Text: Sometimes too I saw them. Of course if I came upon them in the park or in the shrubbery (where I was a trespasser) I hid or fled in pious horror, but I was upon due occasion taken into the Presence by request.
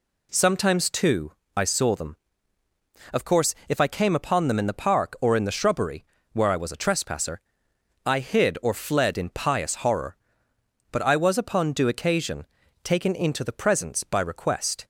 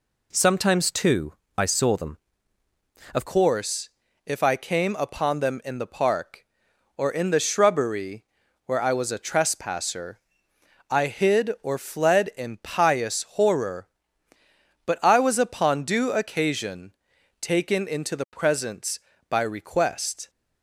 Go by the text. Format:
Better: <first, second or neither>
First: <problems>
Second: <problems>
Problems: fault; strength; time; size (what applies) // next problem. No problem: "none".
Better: first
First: pauses between "too" and "I"; slight; at 1.3 s; 0.24 s long // pauses between "course" and "if"; slight; at 3.5 s; 0.16 s long // pauses between "occasion" and "taken"; at 12.4 s; 0.38 s long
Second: pauses between "too" and "I"; slight; at 1.3 s; 0.24 s long // changes voice at "course"; from 3.2 s on; 17.0 s long // pauses between "course" and "if"; slight; at 3.8 s; 0.34 s long // pauses between "occasion" and "taken"; noticeable; at 16.9 s; 0.48 s long